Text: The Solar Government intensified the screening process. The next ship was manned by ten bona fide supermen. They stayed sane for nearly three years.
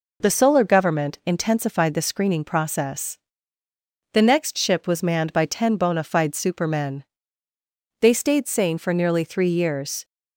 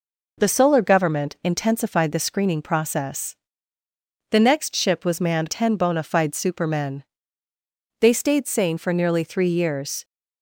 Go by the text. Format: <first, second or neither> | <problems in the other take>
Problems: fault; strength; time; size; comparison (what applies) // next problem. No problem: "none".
first | skips "by"; at 5.4 s